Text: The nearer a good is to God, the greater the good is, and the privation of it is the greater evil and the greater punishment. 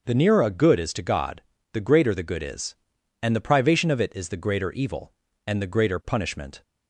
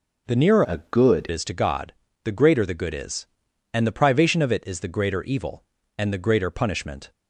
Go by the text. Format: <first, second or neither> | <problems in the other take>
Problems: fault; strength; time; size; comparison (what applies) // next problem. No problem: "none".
first | changes voice from "a" to "good"; from 0.6 to 1.2 s; 0.6 s long